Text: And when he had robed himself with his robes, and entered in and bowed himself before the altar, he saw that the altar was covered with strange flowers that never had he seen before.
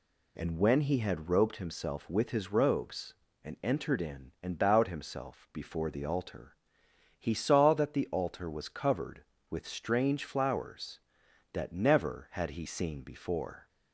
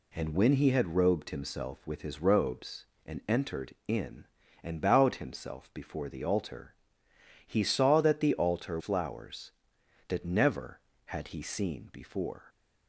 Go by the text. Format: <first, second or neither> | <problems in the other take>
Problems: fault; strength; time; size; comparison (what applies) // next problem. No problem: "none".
first | skips "was covered with strange"; at 8.7 s